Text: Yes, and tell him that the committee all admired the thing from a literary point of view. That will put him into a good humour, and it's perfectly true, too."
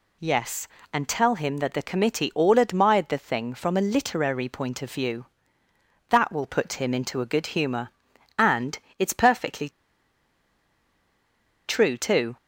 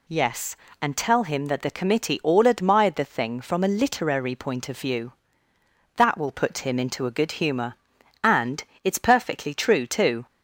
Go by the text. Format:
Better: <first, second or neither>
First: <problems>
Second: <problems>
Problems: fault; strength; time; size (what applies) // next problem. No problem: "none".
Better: second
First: pauses between "and" and "it's"; slight; at 8.7 s; 0.22 s long // pauses between "perfectly" and "true"; strong; at 9.6 s; 1.9 s long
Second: pauses between "and" and "it's"; slight; at 8.6 s; 0.22 s long